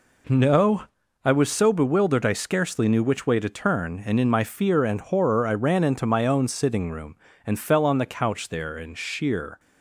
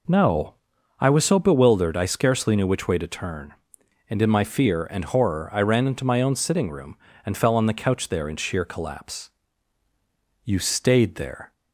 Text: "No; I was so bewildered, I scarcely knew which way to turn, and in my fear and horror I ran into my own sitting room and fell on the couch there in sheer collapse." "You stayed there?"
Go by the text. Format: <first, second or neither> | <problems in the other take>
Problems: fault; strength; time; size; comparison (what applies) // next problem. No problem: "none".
second | stops before "collapse You stayed there"; at 9.5 s